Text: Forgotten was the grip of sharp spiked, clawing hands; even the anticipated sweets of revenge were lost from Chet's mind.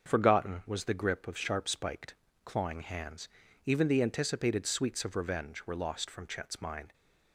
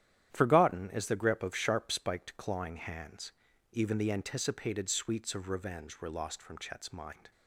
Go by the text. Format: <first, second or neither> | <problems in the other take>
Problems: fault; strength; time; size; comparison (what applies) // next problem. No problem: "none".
first | starts louder than the rest; strong; until 1.3 s; 11 dB; also in the first // says "is" for "was"; at 0.9 s